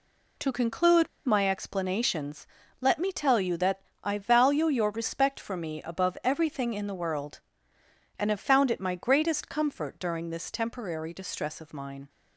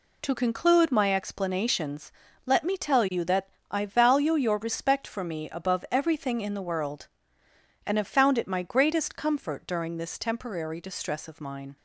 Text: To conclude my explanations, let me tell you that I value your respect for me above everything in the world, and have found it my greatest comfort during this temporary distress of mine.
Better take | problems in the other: second | pauses between "conclude" and "my"; slight; at 1.0 s; 0.18 s long // pauses between "that" and "I"; slight; at 3.8 s; 0.22 s long; slight in the second

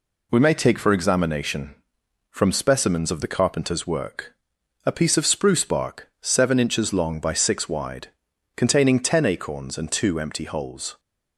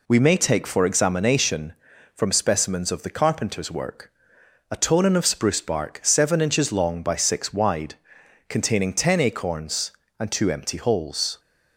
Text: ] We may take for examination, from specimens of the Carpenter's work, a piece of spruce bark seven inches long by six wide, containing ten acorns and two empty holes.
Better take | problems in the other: first | says "tonin" for "piece"; at 4.7 s

